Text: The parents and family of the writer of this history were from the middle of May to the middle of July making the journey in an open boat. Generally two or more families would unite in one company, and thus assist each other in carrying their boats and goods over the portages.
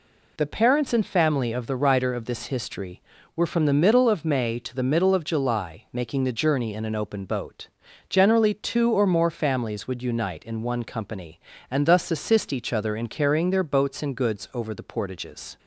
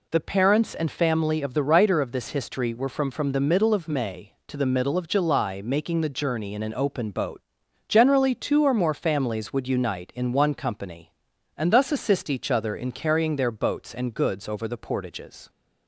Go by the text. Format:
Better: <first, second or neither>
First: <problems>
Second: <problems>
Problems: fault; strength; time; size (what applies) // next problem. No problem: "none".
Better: first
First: none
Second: says "from" twice; at 3.0 s